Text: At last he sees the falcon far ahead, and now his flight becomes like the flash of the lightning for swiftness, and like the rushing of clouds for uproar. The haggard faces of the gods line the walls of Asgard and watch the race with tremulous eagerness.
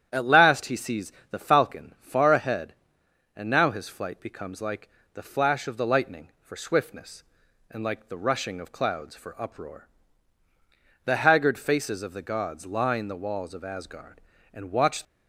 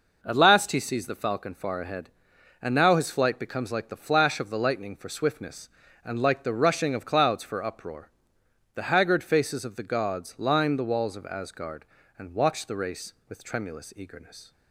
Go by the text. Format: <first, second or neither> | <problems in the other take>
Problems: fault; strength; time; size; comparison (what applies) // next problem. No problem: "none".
second | starts louder than the rest; strong; until 1.1 s; 10 dB // pauses between "sees" and "the"; slight; at 1.1 s; 0.20 s long // pauses between "like" and "the"; slight; at 4.8 s; 0.24 s long // stops before "the race with tremulous eagerness"; at 15.0 s